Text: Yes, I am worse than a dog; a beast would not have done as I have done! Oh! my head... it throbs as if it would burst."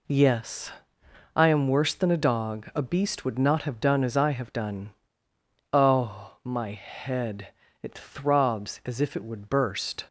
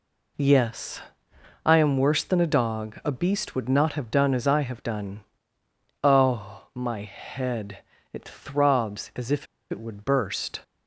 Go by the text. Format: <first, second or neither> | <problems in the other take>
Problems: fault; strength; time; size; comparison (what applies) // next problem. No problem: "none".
first | pauses between "if" and "it"; slight; at 9.4 s; 0.24 s long